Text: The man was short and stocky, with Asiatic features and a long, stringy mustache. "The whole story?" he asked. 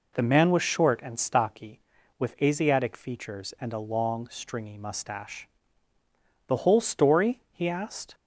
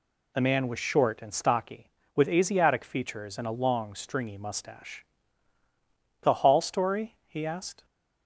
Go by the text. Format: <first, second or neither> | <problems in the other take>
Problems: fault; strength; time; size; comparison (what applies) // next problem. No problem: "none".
first | says "hall" for "whole"; at 6.3 s